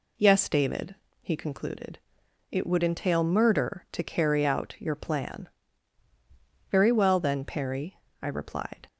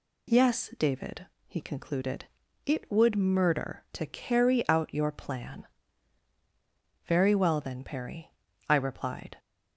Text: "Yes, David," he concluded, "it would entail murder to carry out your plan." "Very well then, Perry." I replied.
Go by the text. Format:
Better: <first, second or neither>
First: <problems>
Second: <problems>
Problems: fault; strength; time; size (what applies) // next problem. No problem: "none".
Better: first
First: none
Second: skips "entail"; at 3.1 s